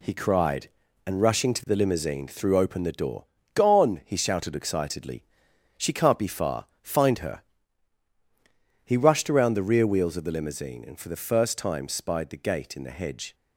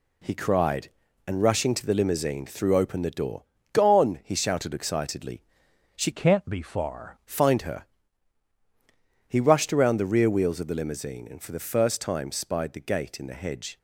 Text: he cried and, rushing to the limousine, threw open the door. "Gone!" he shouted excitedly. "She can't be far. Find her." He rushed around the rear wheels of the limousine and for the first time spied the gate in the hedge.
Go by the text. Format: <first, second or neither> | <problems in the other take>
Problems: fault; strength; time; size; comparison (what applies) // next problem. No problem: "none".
first | changes voice from "can't" to "far"; from 6.1 to 7.1 s; 1.0 s long